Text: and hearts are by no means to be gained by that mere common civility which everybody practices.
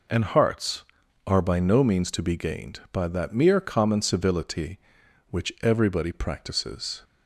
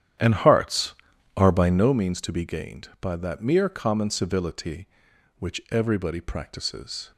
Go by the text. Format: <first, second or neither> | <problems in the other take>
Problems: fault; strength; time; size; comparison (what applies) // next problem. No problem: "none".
first | starts louder than the rest; strong; until 1.9 s; 10 dB